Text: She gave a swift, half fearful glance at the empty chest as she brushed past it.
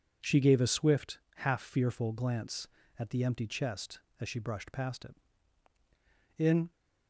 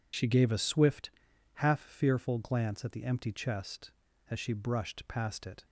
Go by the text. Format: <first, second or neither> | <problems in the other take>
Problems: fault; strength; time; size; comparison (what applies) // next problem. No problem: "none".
second | goes on to say "In"; slight; from 6.3 s on; 0.34 s long